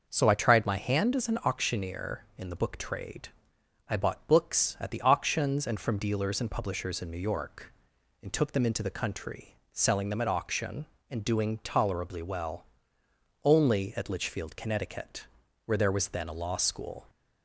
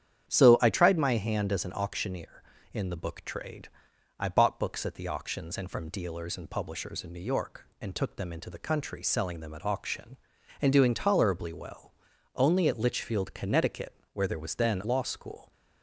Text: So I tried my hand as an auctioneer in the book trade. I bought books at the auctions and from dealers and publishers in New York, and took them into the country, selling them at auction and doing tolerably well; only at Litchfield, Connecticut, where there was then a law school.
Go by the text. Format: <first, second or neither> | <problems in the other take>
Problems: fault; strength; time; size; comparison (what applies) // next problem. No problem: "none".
first | starts louder than the rest; strong; until 1.3 s; 9 dB // skips "a"; at 14.8 s